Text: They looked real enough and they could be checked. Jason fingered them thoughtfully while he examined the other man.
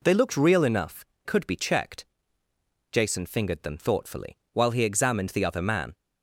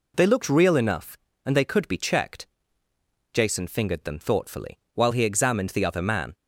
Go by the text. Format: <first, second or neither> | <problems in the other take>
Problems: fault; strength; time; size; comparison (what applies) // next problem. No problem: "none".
second | skips "and they"; at 1.1 s // pauses between "thoughtfully" and "while"; slight; at 4.3 s; 0.16 s long; slight in the second